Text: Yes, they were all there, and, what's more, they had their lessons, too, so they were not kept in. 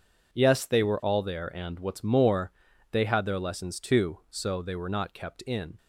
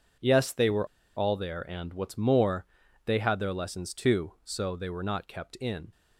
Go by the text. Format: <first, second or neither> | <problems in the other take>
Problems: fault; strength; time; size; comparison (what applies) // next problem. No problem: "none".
first | pauses between "were" and "all"; slight; at 0.8 s; 0.29 s long